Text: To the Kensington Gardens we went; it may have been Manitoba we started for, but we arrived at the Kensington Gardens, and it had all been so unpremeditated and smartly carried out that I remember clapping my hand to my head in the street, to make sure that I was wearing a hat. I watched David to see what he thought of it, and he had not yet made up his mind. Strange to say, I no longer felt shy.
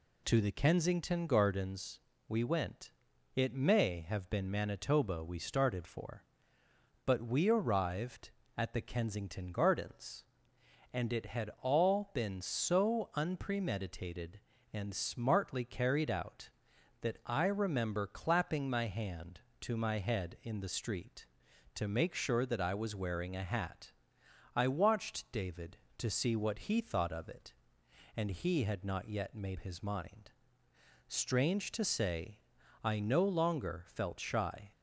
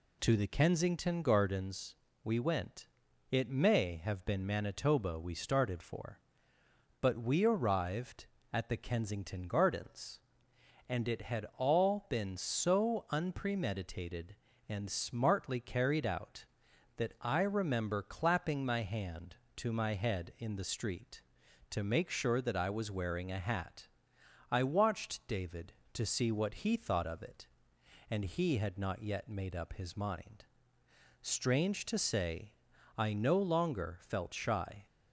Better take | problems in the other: second | pauses between "Gardens" and "we"; slight; at 1.9 s; 0.30 s long; slight in the second // skips "up"; at 29.5 s

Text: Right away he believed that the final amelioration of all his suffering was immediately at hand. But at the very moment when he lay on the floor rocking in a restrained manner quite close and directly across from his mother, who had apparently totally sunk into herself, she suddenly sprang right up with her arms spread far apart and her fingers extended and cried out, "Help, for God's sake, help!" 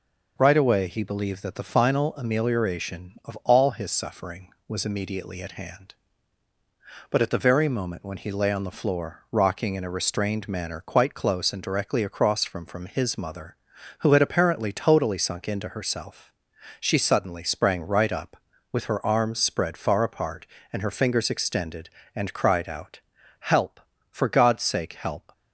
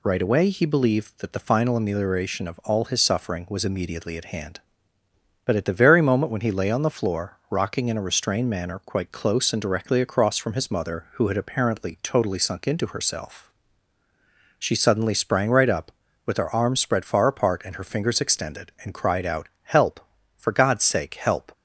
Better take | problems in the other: second | says "from" twice; at 12.6 s

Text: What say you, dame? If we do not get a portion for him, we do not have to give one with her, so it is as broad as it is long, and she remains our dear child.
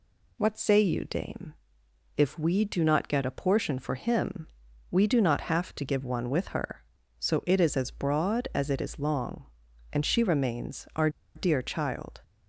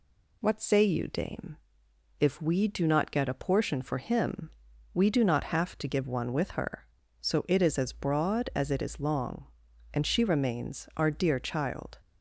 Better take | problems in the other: second | pauses between "our" and "dear"; slight; at 11.0 s; 0.26 s long

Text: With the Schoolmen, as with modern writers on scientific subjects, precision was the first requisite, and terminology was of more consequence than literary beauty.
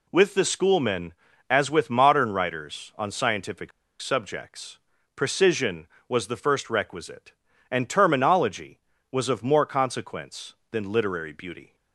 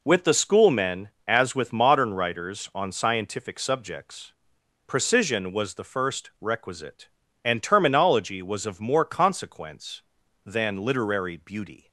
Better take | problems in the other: second | pauses between "scientific" and "subjects"; slight; at 3.7 s; 0.30 s long

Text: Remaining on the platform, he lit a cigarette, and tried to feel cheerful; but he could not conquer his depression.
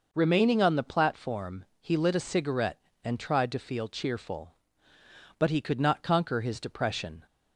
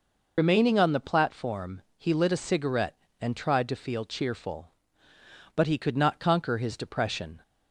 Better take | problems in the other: first | loses the start of "Remaining"; at 0.3 s; 80 ms

